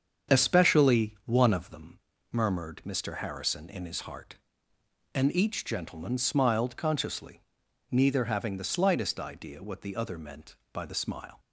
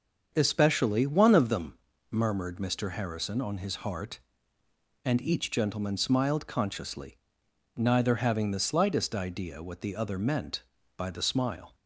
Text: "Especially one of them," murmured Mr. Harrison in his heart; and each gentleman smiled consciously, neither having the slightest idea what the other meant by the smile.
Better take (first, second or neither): first